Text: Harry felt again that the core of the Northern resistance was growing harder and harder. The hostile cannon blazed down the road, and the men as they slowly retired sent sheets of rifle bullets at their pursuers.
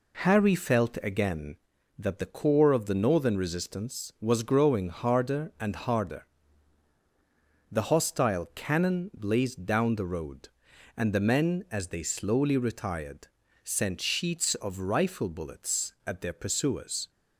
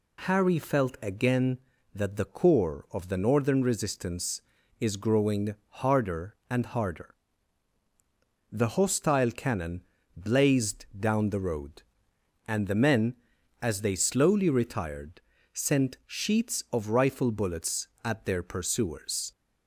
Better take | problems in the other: first | says "is" for "was"; at 4.7 s // pauses between "growing" and "harder"; slight; at 5.5 s; 0.26 s long // pauses between "cannon" and "blazed"; slight; at 9.8 s; 0.34 s long // pauses between "retired" and "sent"; slight; at 15.2 s; 0.32 s long; slight in the first

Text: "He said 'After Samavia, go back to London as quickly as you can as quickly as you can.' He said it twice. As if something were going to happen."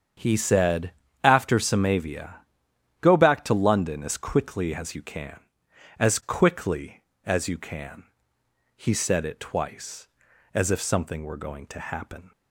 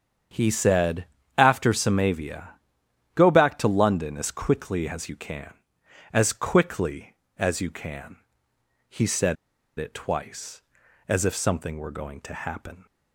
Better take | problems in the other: first | starts louder than the rest; strong; until 1.6 s; 7.5 dB; strong in the first // pauses between "said" and "After"; slight; at 1.0 s; 0.32 s long; slight in the first // pauses between "said" and "it"; at 9.3 s; 0.41 s long

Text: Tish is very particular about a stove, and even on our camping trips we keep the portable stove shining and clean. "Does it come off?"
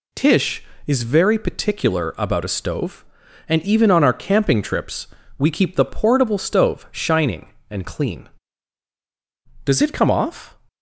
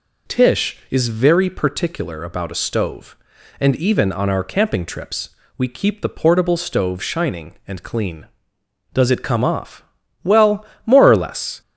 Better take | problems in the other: first | pauses between "trips" and "we"; slight; at 5.3 s; 0.26 s long; slight in the first // goes on to say "Well more or less"; from 10.2 s on; 1.3 s long

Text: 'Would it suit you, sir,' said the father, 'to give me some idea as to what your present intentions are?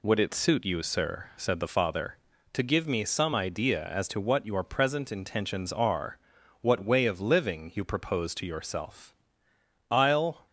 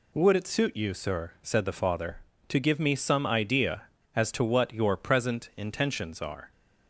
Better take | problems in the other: second | goes on to say "what way of living you propose to yourself I'll"; strong; from 6.5 s on; 3.8 s long

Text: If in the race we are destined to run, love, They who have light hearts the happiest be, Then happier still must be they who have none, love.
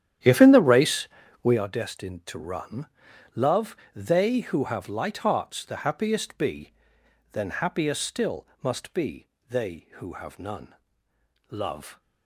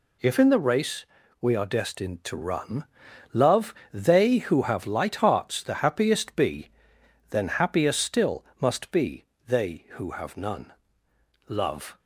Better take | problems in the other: second | starts louder than the rest; strong; until 1.7 s; 10.5 dB // pauses between "race" and "we"; slight; at 1.0 s; 0.36 s long; slight in the second // pauses between "still" and "must"; slight; at 8.4 s; 0.16 s long; slight in the second // pauses between "be" and "they"; slight; at 9.2 s; 0.24 s long; slight in the second

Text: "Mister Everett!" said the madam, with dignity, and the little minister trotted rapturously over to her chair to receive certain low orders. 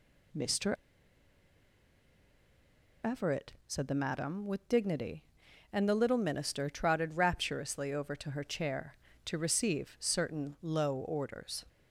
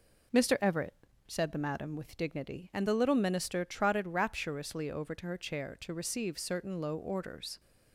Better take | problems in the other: second | pauses between "Mister" and "Everett"; strong; at 0.7 s; 2.3 s long

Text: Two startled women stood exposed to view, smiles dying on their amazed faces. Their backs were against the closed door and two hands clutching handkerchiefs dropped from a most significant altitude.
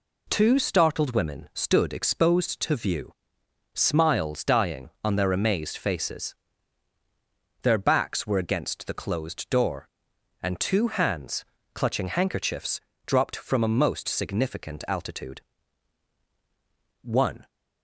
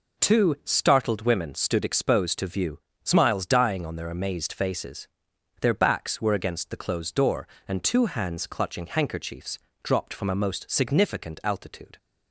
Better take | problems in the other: second | pauses between "hands" and "clutching"; slight; at 11.4 s; 0.30 s long // pauses between "handkerchiefs" and "dropped"; slight; at 12.8 s; 0.26 s long; slight in the second // goes on to say "One"; slight; from 17.0 s on; 0.46 s long

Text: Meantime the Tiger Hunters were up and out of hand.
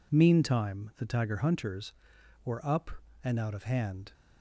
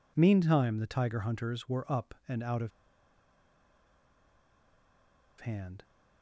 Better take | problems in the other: first | pauses between "of" and "hand"; strong; at 2.7 s; 2.7 s long

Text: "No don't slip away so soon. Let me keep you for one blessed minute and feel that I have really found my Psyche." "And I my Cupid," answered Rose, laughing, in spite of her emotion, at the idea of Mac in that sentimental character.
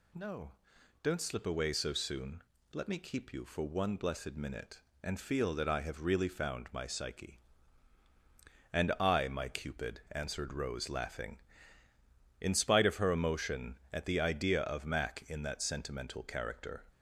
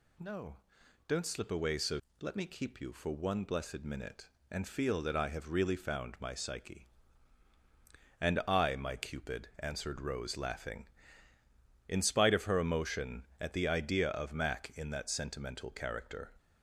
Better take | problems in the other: first | pauses between "No" and "don't"; noticeable; at 0.5 s; 0.50 s long; noticeable in the first // skips "soon"; at 2.0 s

